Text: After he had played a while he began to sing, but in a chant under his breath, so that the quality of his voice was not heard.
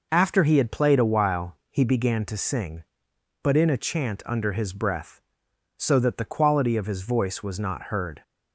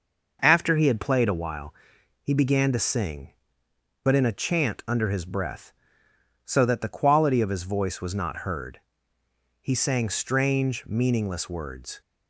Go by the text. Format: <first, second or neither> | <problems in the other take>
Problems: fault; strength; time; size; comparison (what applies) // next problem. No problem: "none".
first | pauses between "while" and "he"; noticeable; at 1.7 s; 0.48 s long // goes on to say "He sang strange meaningless words"; strong; from 9.6 s on; 2.4 s long